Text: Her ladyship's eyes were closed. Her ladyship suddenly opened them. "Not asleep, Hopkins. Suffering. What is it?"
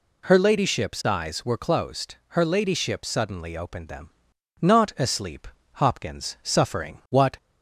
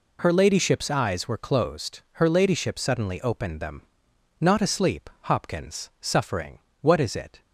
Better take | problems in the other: second | stops before "is it"; at 7.3 s

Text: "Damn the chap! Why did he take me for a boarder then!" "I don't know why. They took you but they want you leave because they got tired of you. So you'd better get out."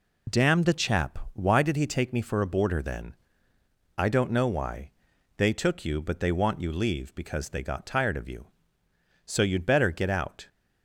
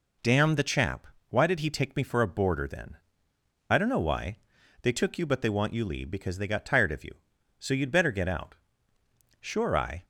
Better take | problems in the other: first | goes on to say "Sure I"; noticeable; from 9.4 s on; 0.62 s long

